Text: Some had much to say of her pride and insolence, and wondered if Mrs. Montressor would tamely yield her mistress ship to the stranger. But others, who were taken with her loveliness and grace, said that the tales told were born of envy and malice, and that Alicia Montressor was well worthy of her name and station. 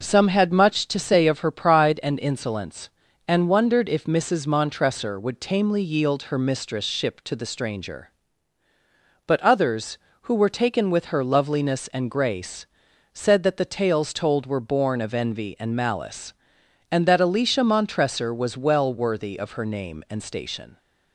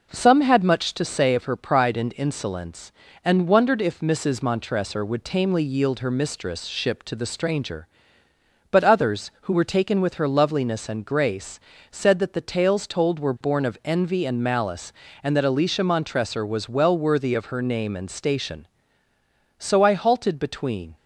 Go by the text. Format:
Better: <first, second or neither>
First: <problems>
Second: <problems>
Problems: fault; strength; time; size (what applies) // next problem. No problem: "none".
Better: first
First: none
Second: goes on to say "So I halted between"; from 19.5 s on; 1.3 s long